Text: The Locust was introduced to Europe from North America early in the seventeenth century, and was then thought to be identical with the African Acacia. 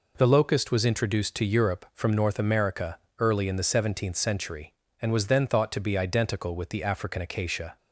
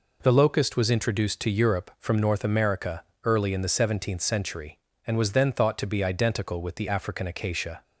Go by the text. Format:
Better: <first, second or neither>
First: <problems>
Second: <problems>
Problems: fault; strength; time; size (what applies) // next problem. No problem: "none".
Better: neither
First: pauses between "America" and "early"; slight; at 2.9 s; 0.20 s long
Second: pauses between "America" and "early"; slight; at 3.0 s; 0.20 s long